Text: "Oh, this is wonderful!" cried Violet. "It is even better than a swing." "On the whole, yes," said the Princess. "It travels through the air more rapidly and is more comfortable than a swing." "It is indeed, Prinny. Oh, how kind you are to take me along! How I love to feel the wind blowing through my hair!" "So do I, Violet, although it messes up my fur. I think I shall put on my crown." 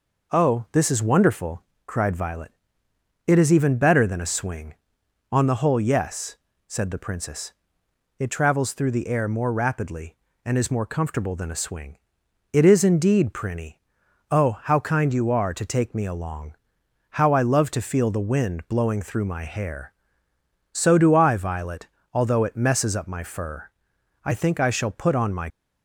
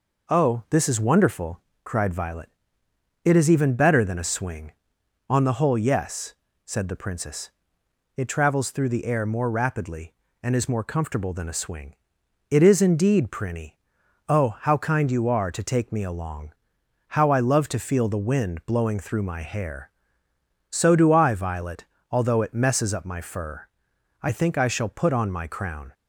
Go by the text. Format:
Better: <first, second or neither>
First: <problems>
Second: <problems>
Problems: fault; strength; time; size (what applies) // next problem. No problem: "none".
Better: second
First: stops before "crown"; at 25.4 s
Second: none